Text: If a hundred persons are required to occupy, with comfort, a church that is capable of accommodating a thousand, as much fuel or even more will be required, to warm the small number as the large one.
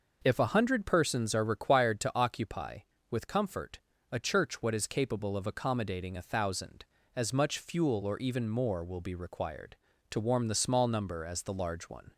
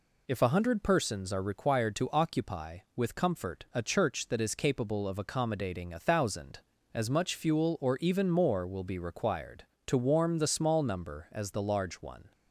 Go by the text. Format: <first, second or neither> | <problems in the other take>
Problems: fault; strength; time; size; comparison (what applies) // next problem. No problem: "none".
second | says "what" for "that"; at 4.6 s